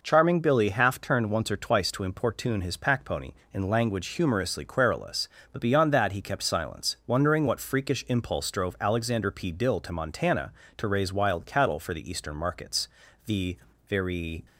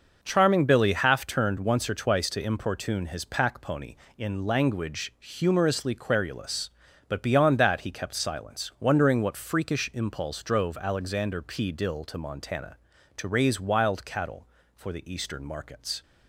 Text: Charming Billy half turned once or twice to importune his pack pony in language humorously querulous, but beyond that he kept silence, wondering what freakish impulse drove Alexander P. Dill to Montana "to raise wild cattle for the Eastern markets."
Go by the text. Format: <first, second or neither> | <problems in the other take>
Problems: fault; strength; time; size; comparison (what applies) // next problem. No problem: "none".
second | goes on to say "The very"; noticeable; from 13.2 s on; 1.2 s long